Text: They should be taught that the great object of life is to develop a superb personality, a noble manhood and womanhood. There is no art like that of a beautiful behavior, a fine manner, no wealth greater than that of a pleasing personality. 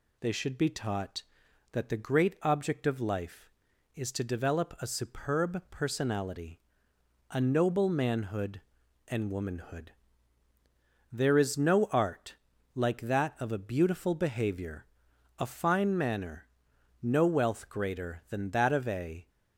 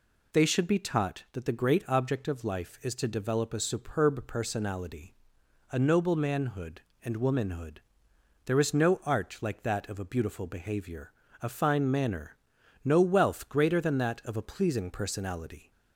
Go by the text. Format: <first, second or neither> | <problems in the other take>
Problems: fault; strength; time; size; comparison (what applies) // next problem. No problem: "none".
second | pauses between "art" and "like"; at 12.3 s; 0.40 s long // stops before "pleasing personality"; at 19.2 s